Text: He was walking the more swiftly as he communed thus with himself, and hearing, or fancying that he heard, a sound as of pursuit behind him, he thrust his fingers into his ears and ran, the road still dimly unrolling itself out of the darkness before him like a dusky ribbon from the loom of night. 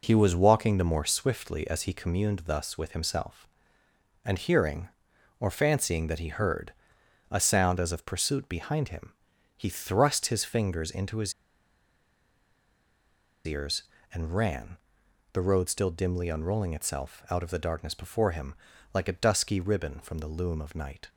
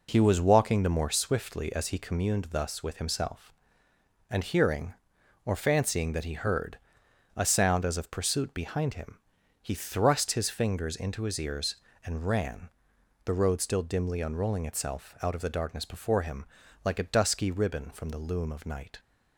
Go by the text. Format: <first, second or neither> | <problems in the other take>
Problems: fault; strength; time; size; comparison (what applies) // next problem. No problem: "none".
second | pauses between "his" and "ears"; strong; at 11.3 s; 2.1 s long // pauses between "him" and "like"; at 18.5 s; 0.40 s long; also in the second